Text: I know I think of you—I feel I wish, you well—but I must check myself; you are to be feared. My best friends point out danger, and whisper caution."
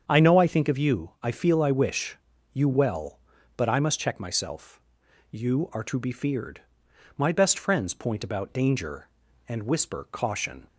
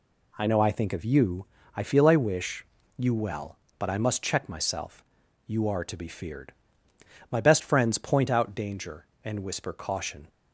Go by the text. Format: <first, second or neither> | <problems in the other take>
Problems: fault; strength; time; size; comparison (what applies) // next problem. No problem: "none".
second | starts louder than the rest; strong; until 1.0 s; 7.5 dB // says "about" for "out"; at 8.2 s